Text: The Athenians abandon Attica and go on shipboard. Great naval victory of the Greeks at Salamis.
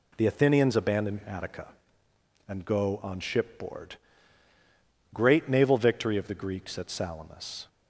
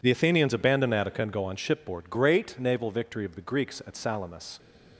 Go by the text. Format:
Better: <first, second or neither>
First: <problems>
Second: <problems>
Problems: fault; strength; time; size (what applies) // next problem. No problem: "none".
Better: neither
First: none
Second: none